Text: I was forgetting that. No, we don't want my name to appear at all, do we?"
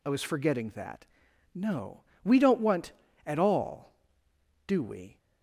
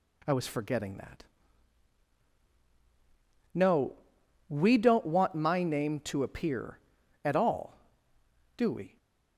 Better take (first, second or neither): second